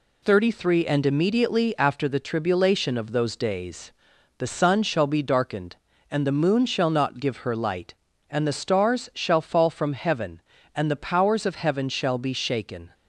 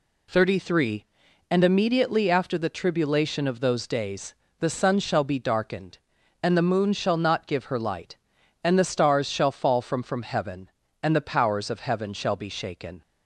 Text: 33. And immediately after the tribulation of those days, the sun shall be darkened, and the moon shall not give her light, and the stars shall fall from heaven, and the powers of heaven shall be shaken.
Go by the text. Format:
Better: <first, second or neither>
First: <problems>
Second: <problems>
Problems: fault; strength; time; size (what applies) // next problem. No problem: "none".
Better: first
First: none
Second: says "from" twice; at 10.0 s